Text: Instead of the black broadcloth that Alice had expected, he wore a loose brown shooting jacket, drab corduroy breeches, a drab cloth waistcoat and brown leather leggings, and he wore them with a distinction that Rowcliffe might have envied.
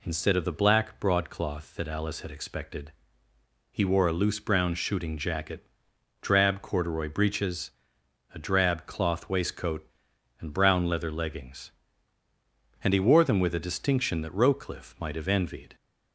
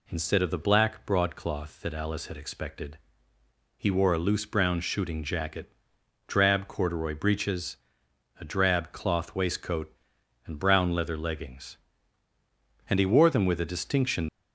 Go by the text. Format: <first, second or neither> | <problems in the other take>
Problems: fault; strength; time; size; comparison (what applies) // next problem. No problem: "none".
first | stops before "that Rowcliffe might have envied"; at 14.2 s